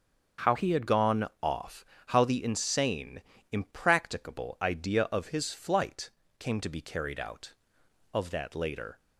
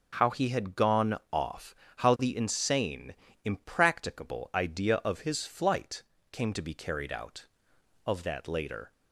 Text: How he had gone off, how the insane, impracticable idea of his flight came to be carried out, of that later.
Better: second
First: starts louder than the rest; until 1.5 s; 6.5 dB // changes voice from "he" to "had"; from 0.5 to 0.8 s; 0.3 s long // pauses between "flight" and "came"; slight; at 6.0 s; 0.28 s long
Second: starts louder than the rest; noticeable; until 1.1 s; 6 dB // pauses between "flight" and "came"; slight; at 6.0 s; 0.28 s long

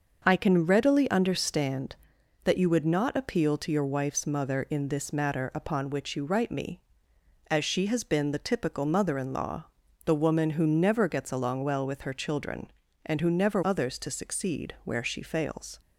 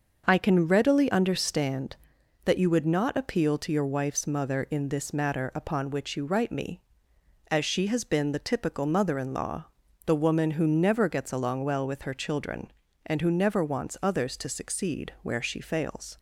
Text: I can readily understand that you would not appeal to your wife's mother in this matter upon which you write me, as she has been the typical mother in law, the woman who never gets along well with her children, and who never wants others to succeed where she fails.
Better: second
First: starts louder than the rest; until 1.2 s; 6 dB // skips "wants"; at 13.6 s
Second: starts louder than the rest; until 1.2 s; 6 dB

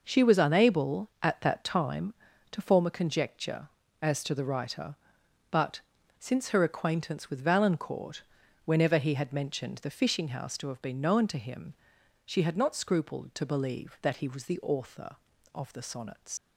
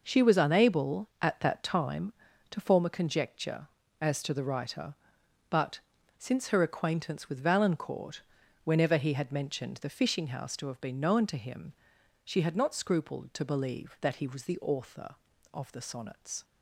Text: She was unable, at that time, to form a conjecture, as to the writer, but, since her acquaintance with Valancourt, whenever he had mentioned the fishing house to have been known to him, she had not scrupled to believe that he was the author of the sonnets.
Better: second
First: leaves "sonnets" unfinished; at 16.3 s; 80 ms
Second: none

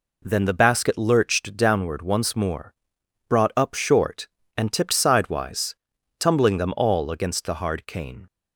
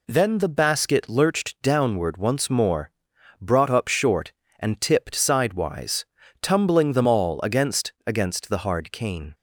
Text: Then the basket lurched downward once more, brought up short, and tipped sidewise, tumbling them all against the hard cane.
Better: first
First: none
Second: says "against" twice; at 8.0 s

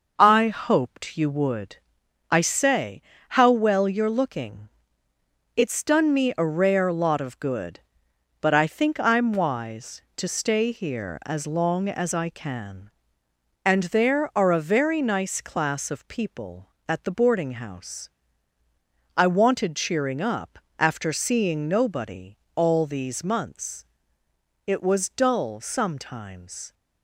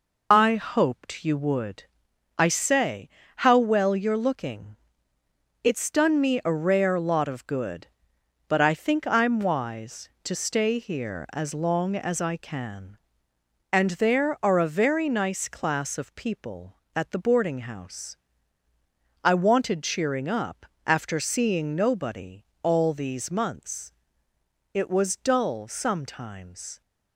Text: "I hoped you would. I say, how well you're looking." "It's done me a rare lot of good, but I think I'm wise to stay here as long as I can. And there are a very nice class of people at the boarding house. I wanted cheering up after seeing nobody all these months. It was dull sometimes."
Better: first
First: pauses between "up" and "after"; slight; at 20.5 s; 0.18 s long // pauses between "nobody" and "all"; slight; at 22.3 s; 0.16 s long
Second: loses the start of "I"; at 0.3 s; 60 ms // pauses between "up" and "after"; slight; at 20.6 s; 0.18 s long // pauses between "nobody" and "all"; slight; at 22.4 s; 0.16 s long

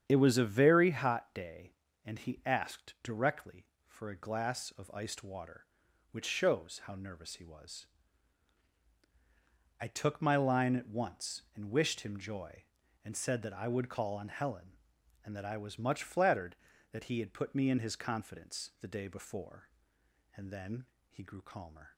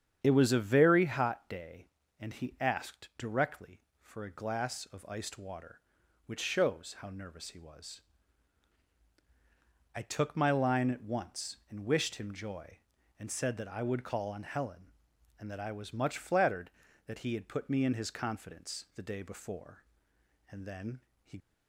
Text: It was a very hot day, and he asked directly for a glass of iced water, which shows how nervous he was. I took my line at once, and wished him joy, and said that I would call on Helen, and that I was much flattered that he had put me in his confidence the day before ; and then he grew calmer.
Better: first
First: starts louder than the rest; strong; until 1.0 s; 8.5 dB // pauses between "then" and "he"; slight; at 20.8 s; 0.26 s long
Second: starts louder than the rest; strong; until 1.2 s; 8.5 dB // pauses between "then" and "he"; slight; at 20.9 s; 0.26 s long // stops before "grew calmer"; at 21.3 s

